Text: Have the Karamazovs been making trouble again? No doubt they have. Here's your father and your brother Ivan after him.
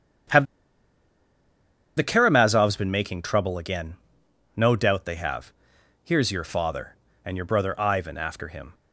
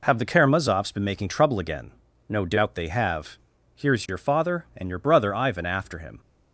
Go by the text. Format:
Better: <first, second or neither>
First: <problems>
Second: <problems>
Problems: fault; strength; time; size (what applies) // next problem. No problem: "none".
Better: second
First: starts louder than the rest; strong; until 2.8 s; 8.5 dB // pauses between "Have" and "the"; strong; at 0.4 s; 1.5 s long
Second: none